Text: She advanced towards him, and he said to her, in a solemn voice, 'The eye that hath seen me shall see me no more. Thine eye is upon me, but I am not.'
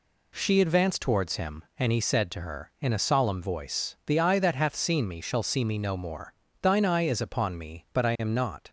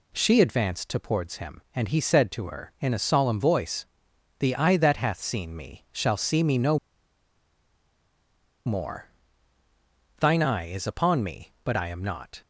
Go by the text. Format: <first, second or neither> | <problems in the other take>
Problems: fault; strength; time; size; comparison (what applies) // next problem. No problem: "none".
first | pauses between "no" and "more"; strong; at 6.7 s; 1.8 s long